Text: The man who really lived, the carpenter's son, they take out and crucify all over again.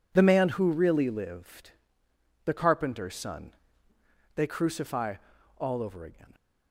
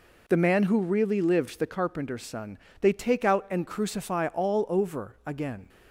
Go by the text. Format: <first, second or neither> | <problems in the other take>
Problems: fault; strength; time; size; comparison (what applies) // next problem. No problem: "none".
second | skips "take out and"; at 4.4 s // pauses between "crucify" and "all"; at 5.1 s; 0.42 s long